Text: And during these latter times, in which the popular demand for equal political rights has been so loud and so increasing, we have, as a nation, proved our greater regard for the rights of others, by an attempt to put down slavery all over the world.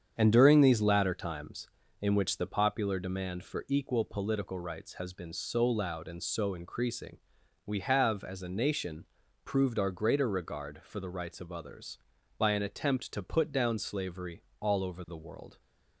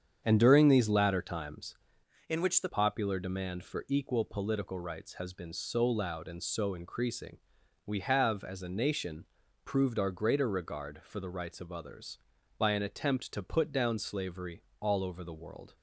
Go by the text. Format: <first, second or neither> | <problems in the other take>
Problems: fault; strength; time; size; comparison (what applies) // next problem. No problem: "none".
first | starts louder than the rest; strong; until 1.2 s; 8 dB; strong in the first // changes voice from "in" to "the"; from 2.2 to 2.6 s; 0.4 s long // pauses between "slavery" and "all"; slight; at 14.6 s; 0.18 s long; slight in the first